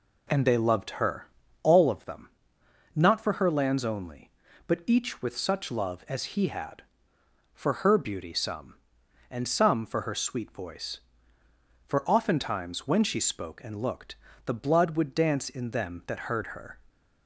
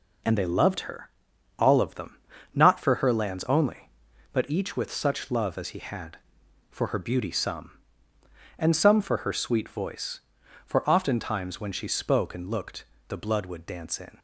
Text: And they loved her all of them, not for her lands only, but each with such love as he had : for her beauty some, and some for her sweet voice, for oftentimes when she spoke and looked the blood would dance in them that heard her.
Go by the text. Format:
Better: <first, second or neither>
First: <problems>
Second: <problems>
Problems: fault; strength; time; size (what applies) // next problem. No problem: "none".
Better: first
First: pauses between "her" and "all"; slight; at 1.2 s; 0.36 s long // pauses between "looked" and "the"; slight; at 14.1 s; 0.30 s long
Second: pauses between "her" and "all"; noticeable; at 1.0 s; 0.49 s long // pauses between "looked" and "the"; slight; at 12.8 s; 0.24 s long // stops before "them that heard her"; at 14.1 s